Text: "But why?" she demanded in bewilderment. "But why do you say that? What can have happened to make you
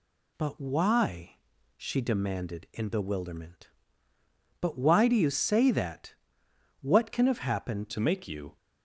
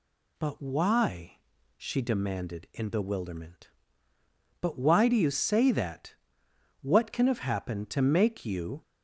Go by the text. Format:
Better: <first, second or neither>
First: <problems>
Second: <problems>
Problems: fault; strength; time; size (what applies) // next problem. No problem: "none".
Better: second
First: changes voice at "to"; from 7.9 s on; 0.6 s long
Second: none